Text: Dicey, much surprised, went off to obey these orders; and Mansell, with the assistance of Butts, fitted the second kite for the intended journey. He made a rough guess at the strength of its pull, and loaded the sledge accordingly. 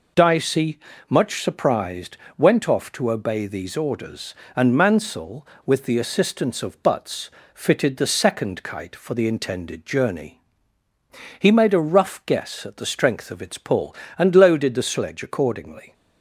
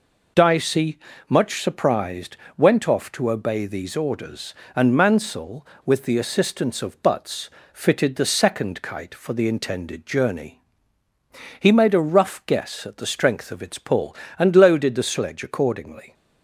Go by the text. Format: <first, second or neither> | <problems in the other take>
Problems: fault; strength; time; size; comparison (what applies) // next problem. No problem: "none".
neither | none